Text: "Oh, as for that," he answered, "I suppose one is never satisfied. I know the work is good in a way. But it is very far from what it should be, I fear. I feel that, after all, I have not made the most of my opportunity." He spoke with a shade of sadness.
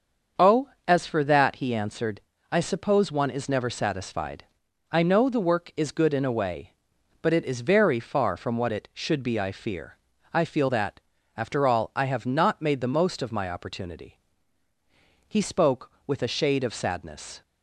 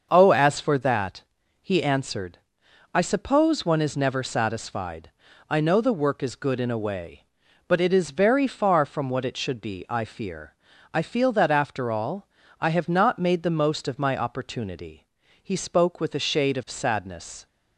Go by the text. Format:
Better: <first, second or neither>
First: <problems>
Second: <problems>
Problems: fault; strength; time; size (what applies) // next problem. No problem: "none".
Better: neither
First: starts louder than the rest; until 1.5 s; 7 dB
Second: starts louder than the rest; until 1.1 s; 6.5 dB